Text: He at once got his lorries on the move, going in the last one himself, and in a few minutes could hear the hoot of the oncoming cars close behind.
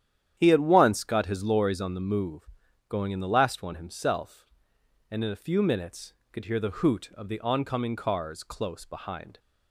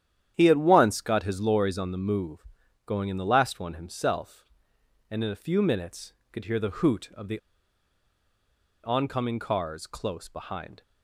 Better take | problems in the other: first | starts louder than the rest; strong; until 1.3 s; 10 dB; strong in the first // pauses between "the" and "oncoming"; strong; at 7.3 s; 1.4 s long

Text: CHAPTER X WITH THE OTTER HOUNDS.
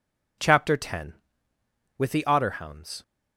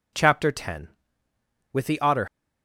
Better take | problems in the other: first | stops before "HOUNDS"; at 2.2 s

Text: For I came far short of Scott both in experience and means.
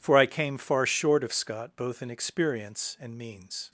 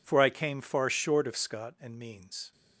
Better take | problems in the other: first | skips "both in experience"; at 1.7 s

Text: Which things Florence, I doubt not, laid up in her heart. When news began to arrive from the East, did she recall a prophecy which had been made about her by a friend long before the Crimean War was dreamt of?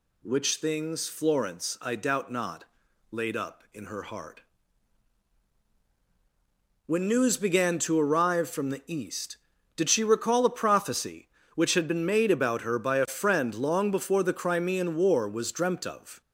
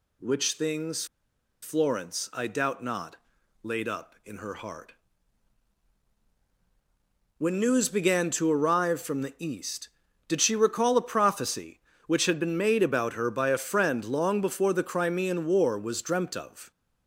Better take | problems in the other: first | pauses between "things" and "Florence"; noticeable; at 1.0 s; 0.56 s long

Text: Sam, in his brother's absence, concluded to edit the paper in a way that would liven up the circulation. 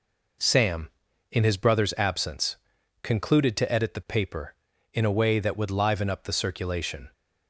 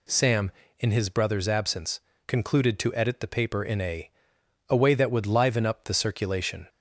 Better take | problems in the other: first | says "a" twice; at 4.6 s

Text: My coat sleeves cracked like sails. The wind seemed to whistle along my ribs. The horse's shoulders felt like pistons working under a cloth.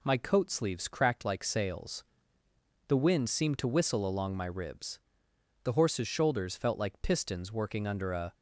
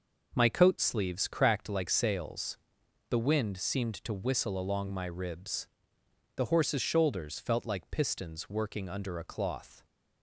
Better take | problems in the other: second | stops before "cloth"; at 8.3 s

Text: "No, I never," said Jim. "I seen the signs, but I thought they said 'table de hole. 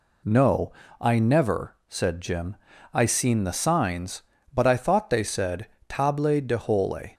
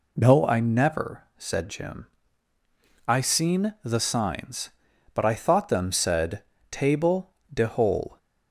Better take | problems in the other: first | says "them" for "they"; at 5.6 s // pauses between "said" and "table"; slight; at 6.4 s; 0.28 s long; slight in the first // pauses between "table" and "de"; slight; at 7.3 s; 0.20 s long

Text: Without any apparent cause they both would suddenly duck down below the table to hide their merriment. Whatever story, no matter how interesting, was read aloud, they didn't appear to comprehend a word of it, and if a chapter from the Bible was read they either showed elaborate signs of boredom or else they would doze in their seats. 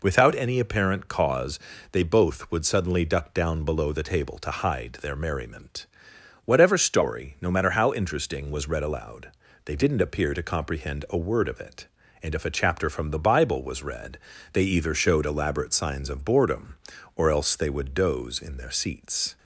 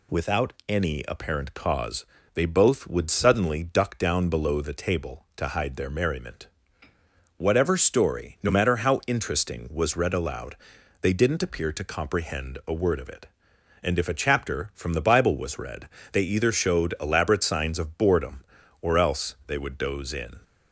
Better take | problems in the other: first | pauses between "Without" and "any"; slight; at 0.5 s; 0.16 s long // pauses between "cause" and "they"; slight; at 2.0 s; 0.30 s long; slight in the first // pauses between "read" and "they"; slight; at 15.8 s; 0.24 s long; slight in the first // stops before "their seats"; at 20.4 s

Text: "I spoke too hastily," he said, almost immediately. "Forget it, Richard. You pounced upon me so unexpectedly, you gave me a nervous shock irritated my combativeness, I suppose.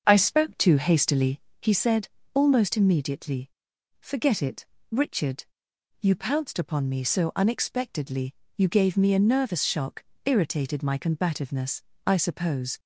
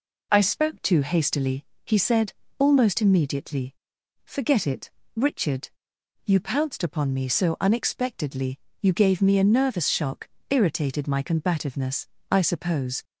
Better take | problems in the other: second | starts louder than the rest; until 1.8 s; 7 dB // pauses between "shock" and "irritated"; slight; at 10.0 s; 0.20 s long; slight in the second

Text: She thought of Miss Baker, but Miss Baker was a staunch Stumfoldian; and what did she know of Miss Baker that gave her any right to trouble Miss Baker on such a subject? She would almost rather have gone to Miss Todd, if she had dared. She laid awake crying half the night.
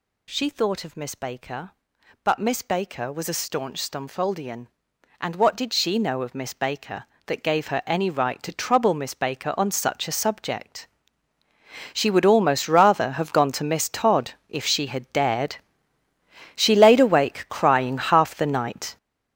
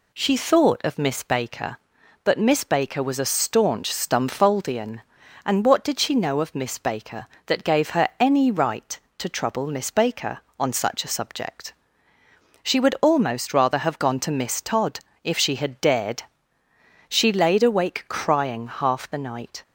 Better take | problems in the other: second | gets louder; strong; throughout; 10 dB

